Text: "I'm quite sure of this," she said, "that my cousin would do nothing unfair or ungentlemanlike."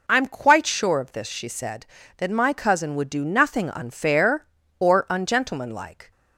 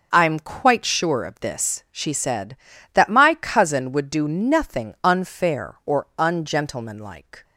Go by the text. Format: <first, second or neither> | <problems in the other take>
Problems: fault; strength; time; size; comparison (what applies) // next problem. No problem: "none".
neither | none